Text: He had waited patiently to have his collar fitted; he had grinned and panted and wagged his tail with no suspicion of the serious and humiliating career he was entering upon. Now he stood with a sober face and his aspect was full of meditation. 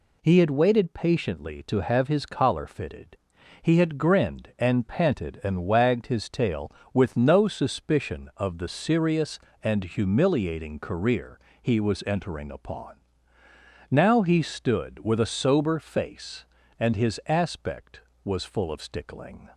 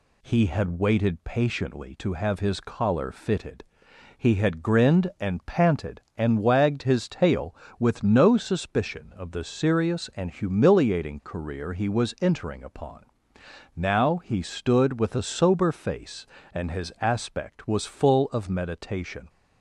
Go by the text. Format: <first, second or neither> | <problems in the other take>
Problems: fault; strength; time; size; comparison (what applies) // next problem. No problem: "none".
second | pauses between "career" and "he"; slight; at 11.3 s; 0.22 s long // says "stickling" for "meditation"; at 18.8 s